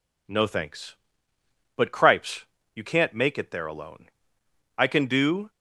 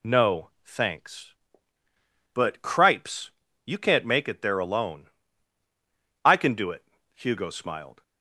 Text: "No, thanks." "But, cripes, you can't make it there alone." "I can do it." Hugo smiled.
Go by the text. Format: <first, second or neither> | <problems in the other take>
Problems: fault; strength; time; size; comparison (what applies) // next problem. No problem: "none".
second | stops before "it Hugo smiled"; at 5.4 s